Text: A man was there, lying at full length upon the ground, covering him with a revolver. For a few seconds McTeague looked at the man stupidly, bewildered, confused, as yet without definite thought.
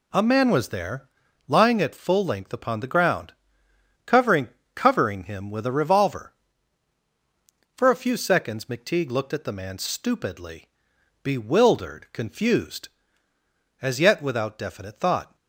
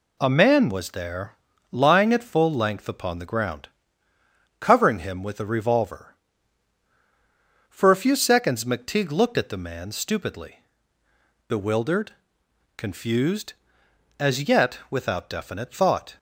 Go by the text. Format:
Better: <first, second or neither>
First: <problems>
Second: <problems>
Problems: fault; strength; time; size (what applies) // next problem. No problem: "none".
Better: second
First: says "covering" twice; at 4.7 s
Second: none